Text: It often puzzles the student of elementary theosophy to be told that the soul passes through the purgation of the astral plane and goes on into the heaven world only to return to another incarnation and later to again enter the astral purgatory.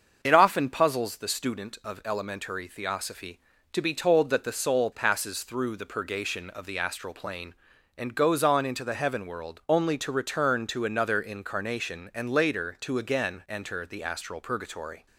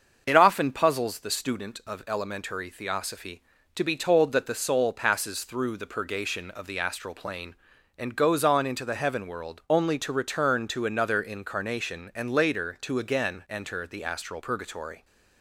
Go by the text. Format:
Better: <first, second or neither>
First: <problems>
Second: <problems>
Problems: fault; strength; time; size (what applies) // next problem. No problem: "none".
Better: neither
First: starts louder than the rest; until 1.2 s; 6.5 dB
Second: starts louder than the rest; until 1.2 s; 6.5 dB